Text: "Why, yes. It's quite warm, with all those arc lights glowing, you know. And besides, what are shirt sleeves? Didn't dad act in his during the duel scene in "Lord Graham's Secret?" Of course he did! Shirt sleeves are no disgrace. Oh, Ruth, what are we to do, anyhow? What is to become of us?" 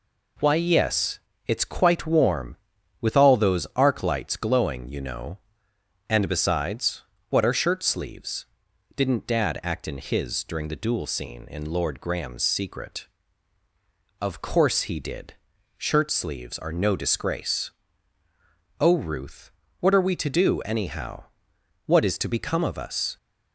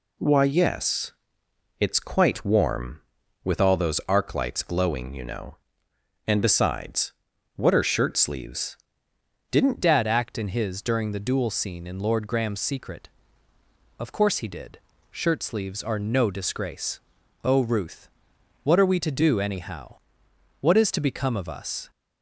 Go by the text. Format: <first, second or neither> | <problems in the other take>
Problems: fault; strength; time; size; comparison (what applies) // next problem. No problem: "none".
first | changes voice at "dad"; from 9.8 s on; 12.0 s long